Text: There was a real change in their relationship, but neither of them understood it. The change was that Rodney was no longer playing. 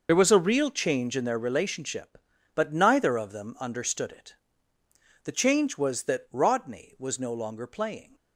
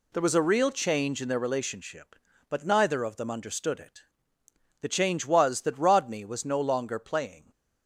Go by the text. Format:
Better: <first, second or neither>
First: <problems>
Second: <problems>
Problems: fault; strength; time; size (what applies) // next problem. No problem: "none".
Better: second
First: loses the start of "There"; at 0.0 s; 45 ms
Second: none